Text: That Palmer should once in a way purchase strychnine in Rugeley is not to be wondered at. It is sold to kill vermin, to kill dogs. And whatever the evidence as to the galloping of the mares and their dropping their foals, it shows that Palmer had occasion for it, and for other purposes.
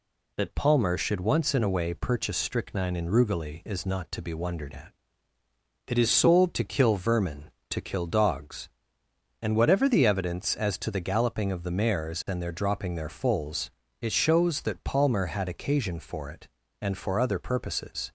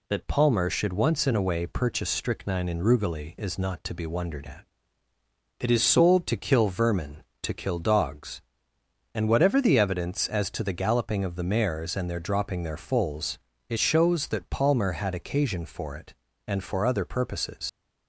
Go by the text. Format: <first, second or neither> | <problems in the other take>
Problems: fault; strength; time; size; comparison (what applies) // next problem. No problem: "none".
first | leaves "purposes" unfinished; at 17.6 s; 85 ms